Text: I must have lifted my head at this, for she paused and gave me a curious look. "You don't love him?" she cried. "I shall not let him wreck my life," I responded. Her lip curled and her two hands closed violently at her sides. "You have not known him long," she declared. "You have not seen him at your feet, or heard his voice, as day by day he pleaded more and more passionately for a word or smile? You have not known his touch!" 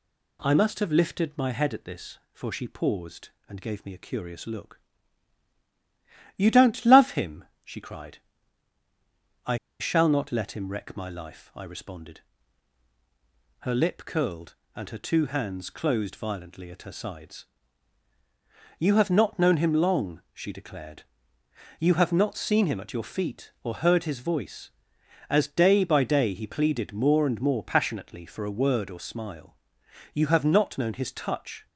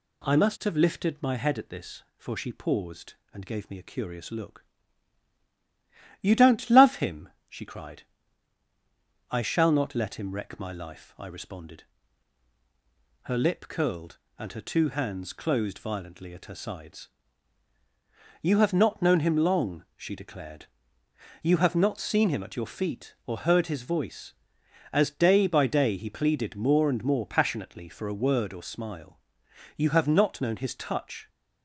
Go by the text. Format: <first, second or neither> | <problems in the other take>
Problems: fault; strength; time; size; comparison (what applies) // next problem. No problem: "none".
second | pauses between "I" and "shall"; slight; at 9.5 s; 0.21 s long